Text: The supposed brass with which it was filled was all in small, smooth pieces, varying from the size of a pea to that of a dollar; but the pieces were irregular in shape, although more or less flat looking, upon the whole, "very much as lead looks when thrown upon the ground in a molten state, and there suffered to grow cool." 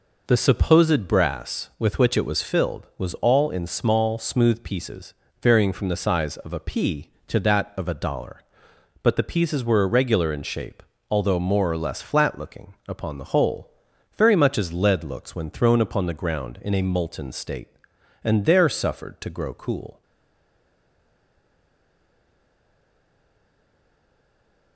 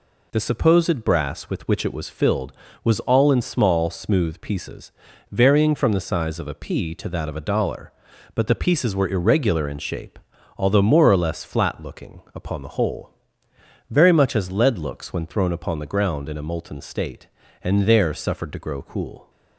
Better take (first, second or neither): second